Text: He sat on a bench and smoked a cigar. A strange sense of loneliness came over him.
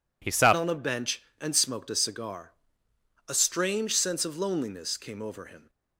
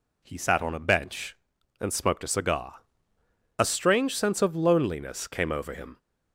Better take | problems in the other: second | changes voice at "on"; from 0.5 s on; 5.1 s long

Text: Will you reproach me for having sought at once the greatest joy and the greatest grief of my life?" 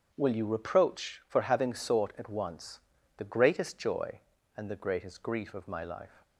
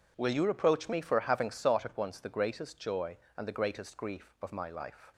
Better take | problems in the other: second | starts louder than the rest; strong; until 1.1 s; 8 dB // skips "me"; at 1.2 s // pauses between "once" and "the"; slight; at 2.8 s; 0.36 s long

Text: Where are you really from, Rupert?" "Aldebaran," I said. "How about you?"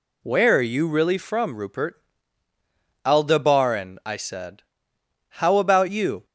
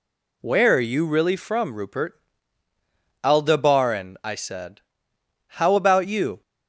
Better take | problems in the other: neither | none

